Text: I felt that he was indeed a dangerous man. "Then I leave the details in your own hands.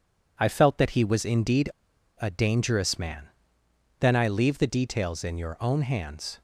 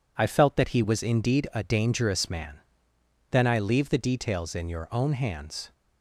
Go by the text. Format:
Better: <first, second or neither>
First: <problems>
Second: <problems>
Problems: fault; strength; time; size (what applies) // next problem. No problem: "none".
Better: second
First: pauses between "indeed" and "a"; noticeable; at 1.6 s; 0.52 s long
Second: none